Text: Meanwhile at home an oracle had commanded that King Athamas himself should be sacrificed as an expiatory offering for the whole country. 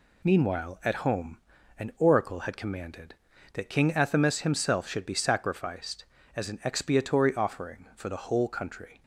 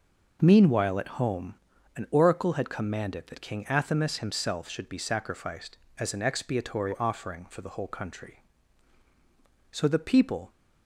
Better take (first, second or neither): first